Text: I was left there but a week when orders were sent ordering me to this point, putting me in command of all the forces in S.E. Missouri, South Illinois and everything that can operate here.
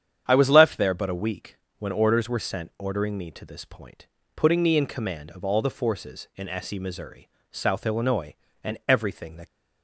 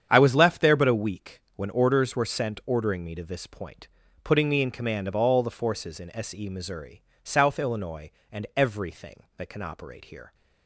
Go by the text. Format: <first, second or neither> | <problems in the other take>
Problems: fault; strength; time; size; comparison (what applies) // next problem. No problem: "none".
second | starts louder than the rest; strong; until 1.2 s; 9 dB; strong in the second // pauses between "week" and "when"; slight; at 1.5 s; 0.22 s long; slight in the second // stops before "can operate here"; at 9.4 s